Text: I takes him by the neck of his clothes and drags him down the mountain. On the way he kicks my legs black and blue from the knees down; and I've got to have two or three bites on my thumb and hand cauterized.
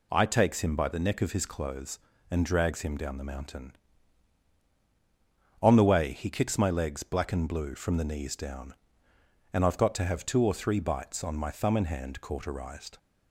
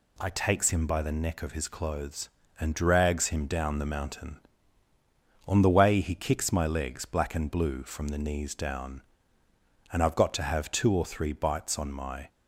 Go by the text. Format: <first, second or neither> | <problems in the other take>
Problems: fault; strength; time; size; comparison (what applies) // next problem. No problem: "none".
first | stops before "thumb and hand cauterized"; at 12.2 s